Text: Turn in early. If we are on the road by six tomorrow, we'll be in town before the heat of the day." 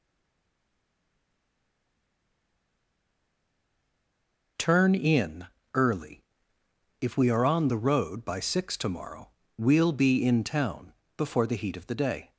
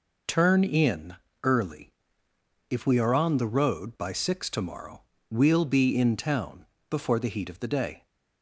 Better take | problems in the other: second | stays silent before the first word; strong; until 4.5 s; 4.5 s long // pauses between "in" and "early"; slight; at 5.4 s; 0.28 s long; slight in the second // pauses between "town" and "before"; slight; at 10.9 s; 0.24 s long; slight in the second

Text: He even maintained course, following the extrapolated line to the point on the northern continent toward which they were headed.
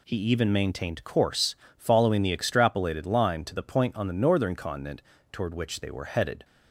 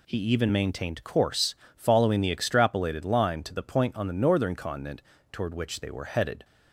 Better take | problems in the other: neither | pauses between "continent" and "toward"; slight; the same in both

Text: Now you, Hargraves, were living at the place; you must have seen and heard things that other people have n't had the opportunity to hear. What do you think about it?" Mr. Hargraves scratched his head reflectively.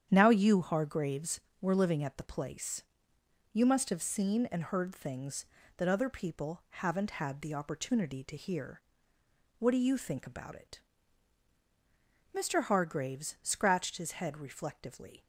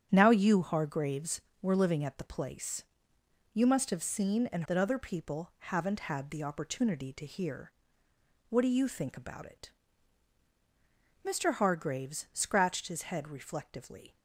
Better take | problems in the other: first | starts louder than the rest; strong; until 1.1 s; 8.5 dB; strong in the first // skips "heard things"; at 4.6 s

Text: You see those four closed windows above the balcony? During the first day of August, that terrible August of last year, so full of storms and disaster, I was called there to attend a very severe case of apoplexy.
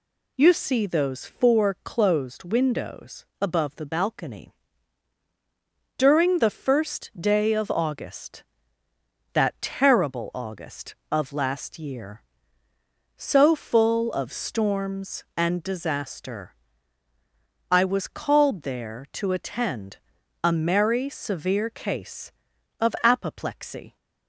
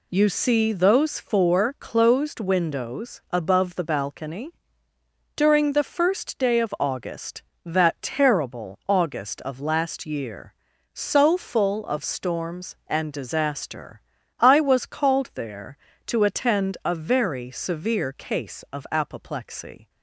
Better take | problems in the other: second | pauses between "windows" and "above"; slight; at 3.2 s; 0.16 s long // pauses between "attend" and "a"; at 19.9 s; 0.44 s long // says "merry" for "very"; at 20.5 s

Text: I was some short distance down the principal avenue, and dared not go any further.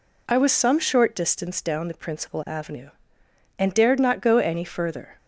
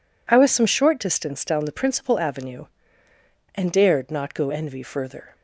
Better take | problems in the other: first | says "envy" for "any"; at 4.4 s

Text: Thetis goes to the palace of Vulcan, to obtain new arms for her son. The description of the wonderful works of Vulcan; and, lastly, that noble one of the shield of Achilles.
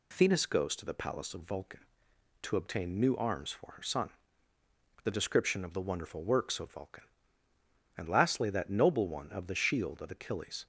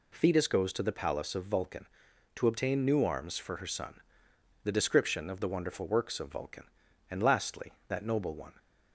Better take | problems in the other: first | stops before "of the shield of Achilles"; at 8.5 s

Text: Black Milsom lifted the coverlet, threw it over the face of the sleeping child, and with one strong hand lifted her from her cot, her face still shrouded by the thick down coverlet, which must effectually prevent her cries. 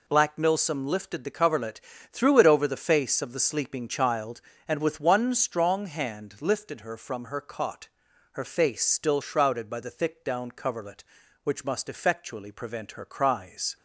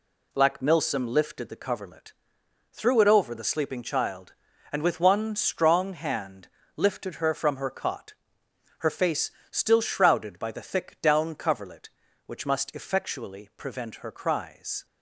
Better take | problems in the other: first | skips "face of the"; at 3.4 s // pauses between "hand" and "lifted"; slight; at 6.4 s; 0.30 s long // pauses between "face" and "still"; slight; at 9.3 s; 0.20 s long

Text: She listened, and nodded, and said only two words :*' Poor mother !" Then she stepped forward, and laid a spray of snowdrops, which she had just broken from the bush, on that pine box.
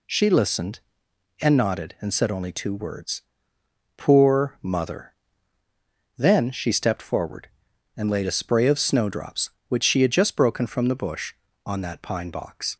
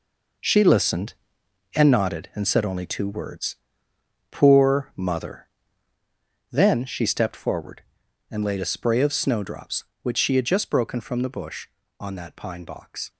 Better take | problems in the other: first | gets quieter; slight; throughout; 2.5 dB

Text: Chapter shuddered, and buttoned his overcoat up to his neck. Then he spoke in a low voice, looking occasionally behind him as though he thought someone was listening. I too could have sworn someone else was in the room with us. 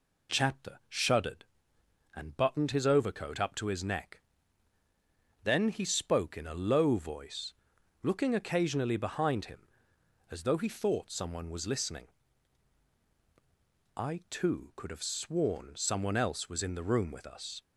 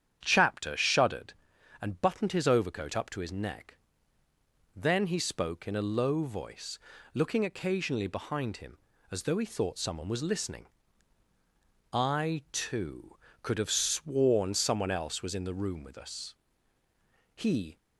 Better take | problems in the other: first | starts louder than the rest; strong; until 1.2 s; 9 dB // goes on to say "He"; slight; from 17.3 s on; 0.44 s long

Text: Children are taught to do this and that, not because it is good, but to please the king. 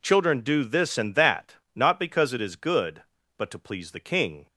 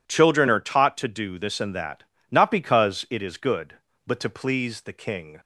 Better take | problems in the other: second | skips "are taught to"; at 0.3 s

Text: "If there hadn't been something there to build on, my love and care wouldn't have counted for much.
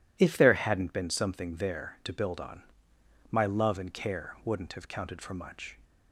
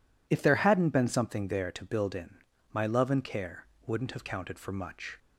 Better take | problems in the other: first | says "in" for "on"; at 2.1 s // pauses between "care" and "wouldn't"; slight; at 3.6 s; 0.20 s long

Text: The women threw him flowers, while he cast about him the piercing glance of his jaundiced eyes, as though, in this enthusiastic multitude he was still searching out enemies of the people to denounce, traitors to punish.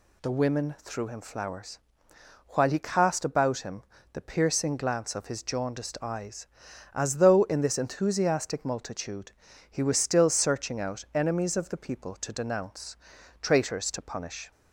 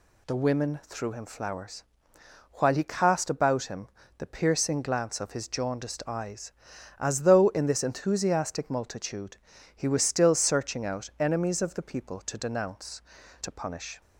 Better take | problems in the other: first | pauses between "him" and "the"; slight; at 3.8 s; 0.30 s long; slight in the first // pauses between "multitude" and "he"; at 9.3 s; 0.40 s long; also in the first // skips "traitors"; at 13.2 s

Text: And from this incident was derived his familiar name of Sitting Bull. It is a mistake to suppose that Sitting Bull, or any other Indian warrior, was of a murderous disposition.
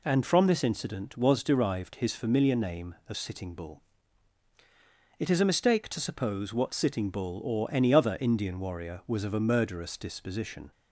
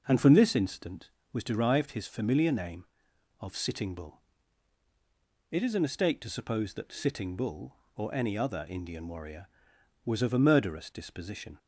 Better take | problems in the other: second | says "what" for "that"; at 6.5 s

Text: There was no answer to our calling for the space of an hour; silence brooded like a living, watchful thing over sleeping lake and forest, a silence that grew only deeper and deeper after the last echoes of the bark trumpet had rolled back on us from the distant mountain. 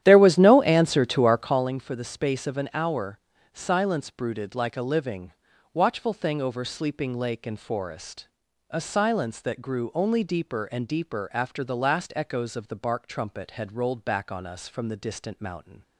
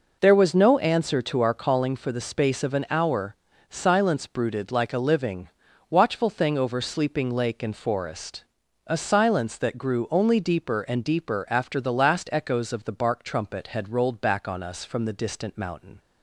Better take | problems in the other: second | starts louder than the rest; strong; until 1.7 s; 11.5 dB

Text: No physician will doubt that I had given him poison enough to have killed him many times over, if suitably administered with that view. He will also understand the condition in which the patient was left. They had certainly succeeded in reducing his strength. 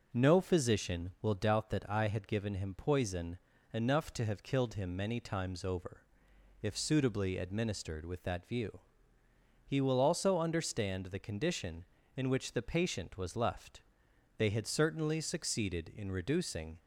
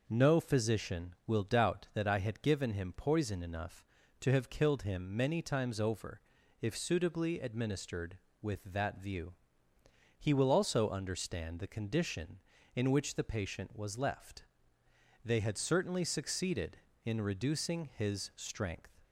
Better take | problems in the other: second | pauses between "poison" and "enough"; at 3.3 s; 0.38 s long // stops before "his strength"; at 16.7 s

